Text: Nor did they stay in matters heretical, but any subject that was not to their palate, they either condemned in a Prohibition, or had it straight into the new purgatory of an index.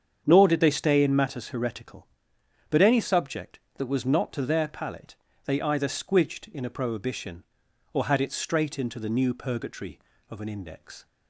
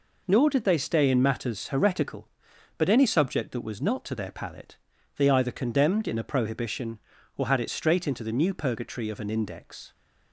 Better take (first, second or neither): second